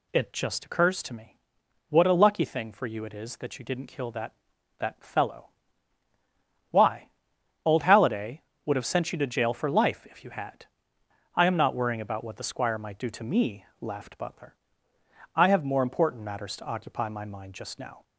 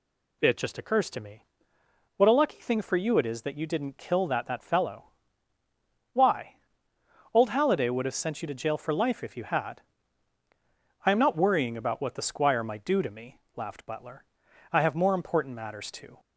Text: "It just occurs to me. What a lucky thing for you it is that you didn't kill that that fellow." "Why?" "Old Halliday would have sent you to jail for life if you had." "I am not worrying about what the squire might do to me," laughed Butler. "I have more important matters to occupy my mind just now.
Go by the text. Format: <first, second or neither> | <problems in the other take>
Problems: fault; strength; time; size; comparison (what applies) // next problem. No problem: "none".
first | stops before "occupy my mind just now"; at 16.1 s